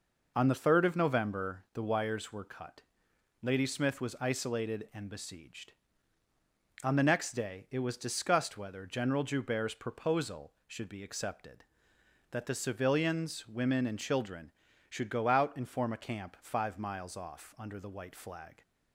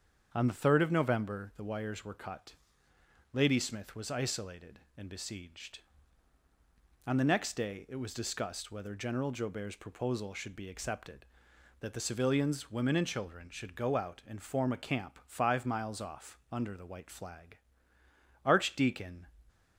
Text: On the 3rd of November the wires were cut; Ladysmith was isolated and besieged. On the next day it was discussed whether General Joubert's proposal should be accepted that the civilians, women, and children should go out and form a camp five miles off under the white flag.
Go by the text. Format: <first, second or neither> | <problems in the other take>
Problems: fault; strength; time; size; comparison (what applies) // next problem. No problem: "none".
first | starts louder than the rest; strong; until 1.3 s; 7.5 dB // goes on to say "Archdeacon"; noticeable; from 18.4 s on; 0.82 s long